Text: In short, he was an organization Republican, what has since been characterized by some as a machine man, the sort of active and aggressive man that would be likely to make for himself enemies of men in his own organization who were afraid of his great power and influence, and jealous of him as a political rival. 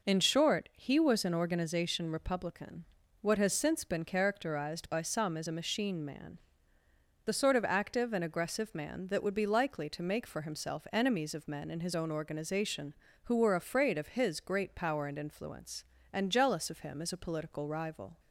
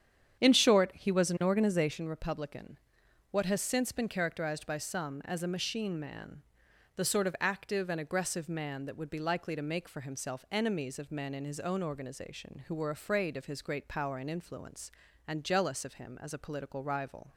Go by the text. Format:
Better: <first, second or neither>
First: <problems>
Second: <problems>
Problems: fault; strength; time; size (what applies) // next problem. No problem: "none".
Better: first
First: none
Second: starts louder than the rest; strong; until 2.0 s; 8.5 dB